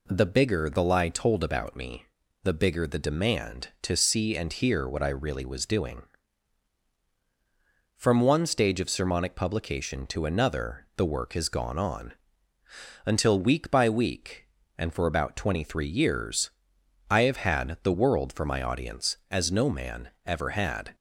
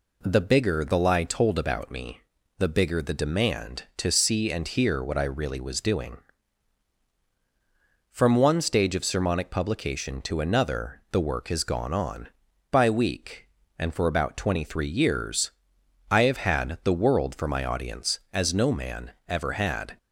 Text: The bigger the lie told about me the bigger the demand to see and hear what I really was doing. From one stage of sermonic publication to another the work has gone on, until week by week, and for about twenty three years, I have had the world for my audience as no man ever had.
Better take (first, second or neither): first